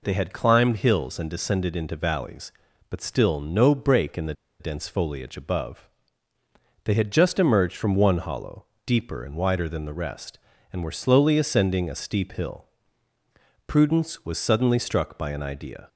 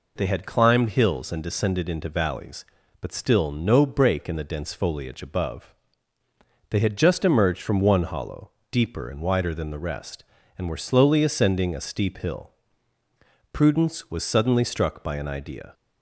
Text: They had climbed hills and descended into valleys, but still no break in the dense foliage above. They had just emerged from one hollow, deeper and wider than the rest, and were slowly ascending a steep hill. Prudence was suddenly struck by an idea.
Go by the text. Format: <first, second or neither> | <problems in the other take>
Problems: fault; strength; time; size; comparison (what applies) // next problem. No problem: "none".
second | pauses between "the" and "dense"; slight; at 4.3 s; 0.26 s long